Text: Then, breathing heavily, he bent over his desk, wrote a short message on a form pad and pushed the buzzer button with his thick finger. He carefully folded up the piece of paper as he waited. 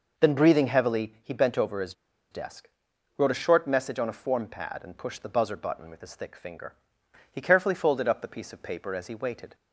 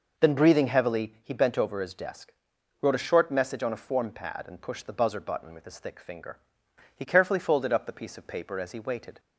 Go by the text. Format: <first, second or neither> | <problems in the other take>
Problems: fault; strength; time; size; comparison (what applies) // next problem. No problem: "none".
second | pauses between "his" and "desk"; at 1.9 s; 0.38 s long